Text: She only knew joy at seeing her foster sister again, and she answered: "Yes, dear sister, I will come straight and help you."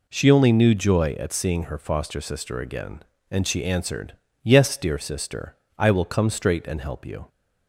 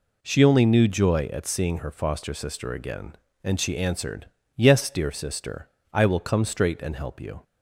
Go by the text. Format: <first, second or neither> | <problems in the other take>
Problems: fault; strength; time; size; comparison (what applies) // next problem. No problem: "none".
neither | none